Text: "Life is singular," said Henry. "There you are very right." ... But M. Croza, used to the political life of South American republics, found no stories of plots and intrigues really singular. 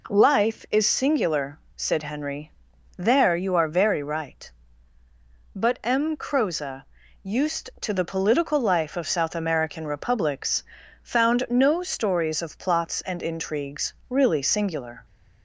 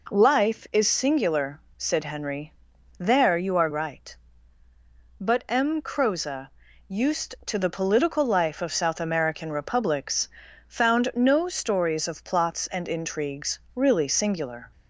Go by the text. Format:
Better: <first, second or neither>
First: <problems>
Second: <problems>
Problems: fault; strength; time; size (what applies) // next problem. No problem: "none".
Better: first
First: pauses between "intrigues" and "really"; slight; at 13.9 s; 0.16 s long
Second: skips "very"; at 3.6 s // pauses between "intrigues" and "really"; slight; at 13.6 s; 0.16 s long